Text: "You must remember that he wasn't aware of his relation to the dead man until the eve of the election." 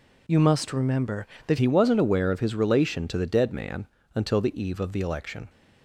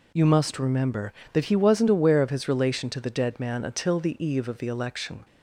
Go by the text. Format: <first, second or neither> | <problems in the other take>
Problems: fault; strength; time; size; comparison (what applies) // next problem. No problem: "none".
second | changes voice at "he"; from 1.5 s on; 3.9 s long // pauses between "man" and "until"; slight; at 3.8 s; 0.30 s long